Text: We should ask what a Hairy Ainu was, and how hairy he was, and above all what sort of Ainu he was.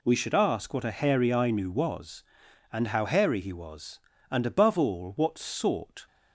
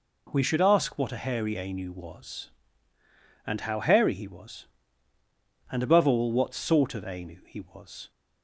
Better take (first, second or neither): second